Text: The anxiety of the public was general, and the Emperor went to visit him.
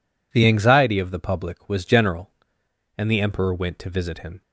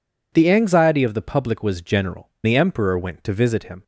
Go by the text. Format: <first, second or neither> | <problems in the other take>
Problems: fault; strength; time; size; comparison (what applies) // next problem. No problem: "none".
first | skips "and"; at 2.3 s